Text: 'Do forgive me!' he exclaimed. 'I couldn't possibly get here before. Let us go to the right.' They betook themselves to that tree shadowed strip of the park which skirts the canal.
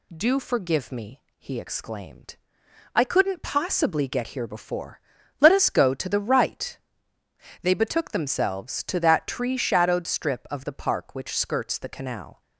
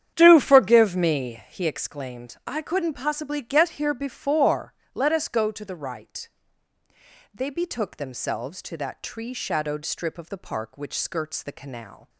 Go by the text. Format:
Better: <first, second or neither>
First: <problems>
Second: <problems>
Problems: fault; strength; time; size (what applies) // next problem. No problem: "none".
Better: first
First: none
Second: starts louder than the rest; strong; until 1.6 s; 9.5 dB